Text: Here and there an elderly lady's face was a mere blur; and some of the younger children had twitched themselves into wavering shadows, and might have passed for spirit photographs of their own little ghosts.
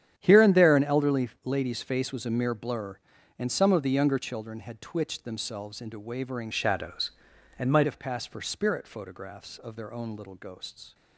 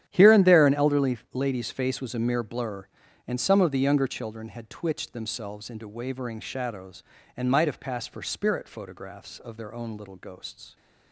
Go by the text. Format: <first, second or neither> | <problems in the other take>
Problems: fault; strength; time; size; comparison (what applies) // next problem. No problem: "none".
second | starts louder than the rest; strong; until 1.1 s; 10 dB; strong in the second // pauses between "elderly" and "lady's"; slight; at 1.2 s; 0.16 s long; slight in the second // changes voice from "shadows" to "might"; from 6.5 to 7.8 s; 1.3 s long